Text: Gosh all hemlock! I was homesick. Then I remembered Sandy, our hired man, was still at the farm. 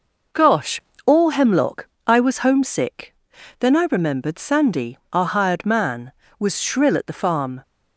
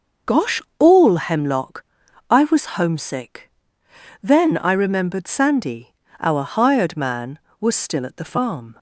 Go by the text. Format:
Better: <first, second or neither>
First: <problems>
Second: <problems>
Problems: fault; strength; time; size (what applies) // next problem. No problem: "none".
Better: second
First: pauses between "Gosh" and "all"; slight; at 0.8 s; 0.24 s long // says "shrill" for "still"; at 6.6 s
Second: pauses between "Gosh" and "all"; slight; at 0.5 s; 0.20 s long